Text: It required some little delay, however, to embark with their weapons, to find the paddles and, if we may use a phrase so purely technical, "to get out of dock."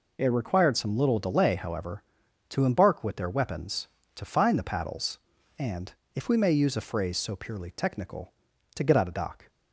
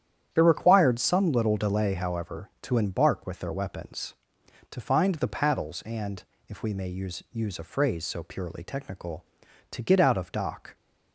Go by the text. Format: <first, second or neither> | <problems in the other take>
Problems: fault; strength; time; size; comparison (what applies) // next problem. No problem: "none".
first | starts louder than the rest; strong; until 1.3 s; 10 dB // says "use" twice; at 7.3 s